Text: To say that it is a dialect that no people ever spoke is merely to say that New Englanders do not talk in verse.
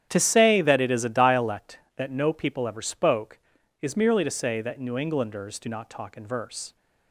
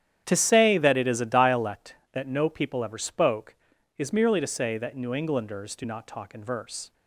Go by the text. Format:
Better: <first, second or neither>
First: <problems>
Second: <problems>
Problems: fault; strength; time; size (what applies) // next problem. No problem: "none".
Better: neither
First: starts louder than the rest; strong; until 1.1 s; 10 dB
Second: starts louder than the rest; strong; until 1.2 s; 10 dB